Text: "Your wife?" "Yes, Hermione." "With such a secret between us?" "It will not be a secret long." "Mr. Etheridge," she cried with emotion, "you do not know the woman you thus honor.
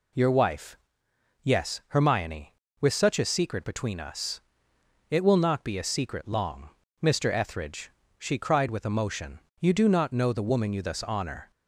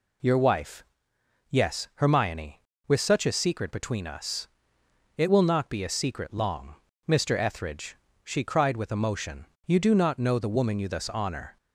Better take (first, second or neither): neither